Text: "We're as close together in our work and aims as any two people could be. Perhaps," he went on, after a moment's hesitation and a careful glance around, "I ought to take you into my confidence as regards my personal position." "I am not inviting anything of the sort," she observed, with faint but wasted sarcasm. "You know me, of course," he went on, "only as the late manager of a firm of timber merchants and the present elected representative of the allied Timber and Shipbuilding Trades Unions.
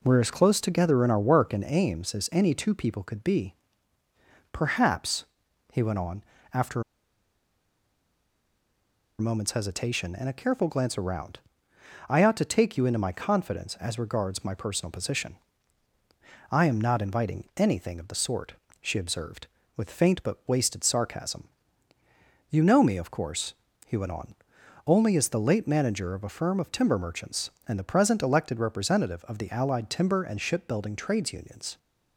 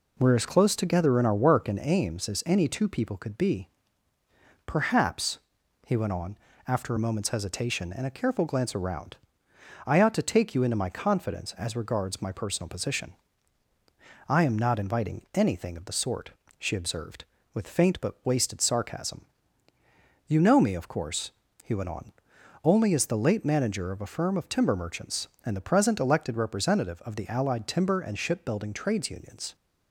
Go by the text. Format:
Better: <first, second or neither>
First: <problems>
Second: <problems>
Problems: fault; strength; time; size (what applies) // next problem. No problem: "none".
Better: second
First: pauses between "after" and "a"; strong; at 6.8 s; 2.3 s long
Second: none